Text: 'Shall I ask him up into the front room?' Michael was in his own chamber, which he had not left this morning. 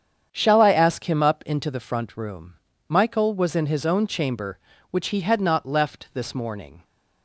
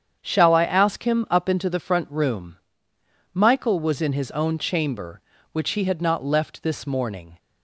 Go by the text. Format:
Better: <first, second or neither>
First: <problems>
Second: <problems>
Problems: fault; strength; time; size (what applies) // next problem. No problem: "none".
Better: neither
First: starts louder than the rest; strong; until 1.3 s; 8 dB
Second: starts louder than the rest; strong; until 1.2 s; 8 dB